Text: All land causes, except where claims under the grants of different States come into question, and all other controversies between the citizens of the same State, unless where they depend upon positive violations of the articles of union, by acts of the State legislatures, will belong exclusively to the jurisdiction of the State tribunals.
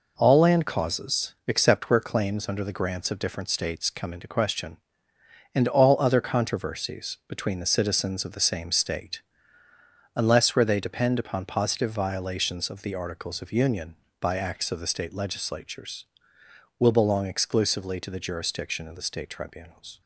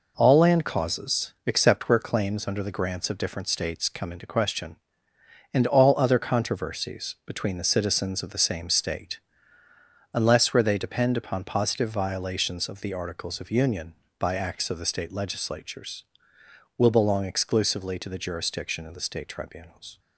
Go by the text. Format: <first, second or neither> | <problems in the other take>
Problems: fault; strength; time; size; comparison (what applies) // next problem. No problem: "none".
neither | none